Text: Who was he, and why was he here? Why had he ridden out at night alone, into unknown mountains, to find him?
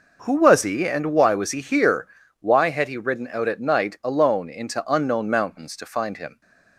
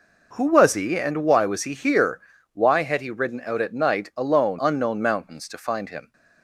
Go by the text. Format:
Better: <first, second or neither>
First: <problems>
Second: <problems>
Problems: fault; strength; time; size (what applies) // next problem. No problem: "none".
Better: first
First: none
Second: skips "into"; at 4.5 s